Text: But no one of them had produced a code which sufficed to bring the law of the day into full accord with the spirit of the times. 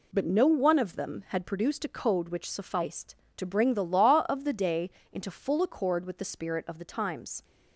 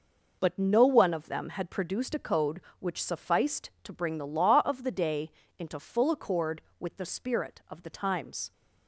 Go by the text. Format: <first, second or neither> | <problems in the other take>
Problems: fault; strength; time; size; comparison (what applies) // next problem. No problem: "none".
neither | pauses between "day" and "into"; slight; the same in both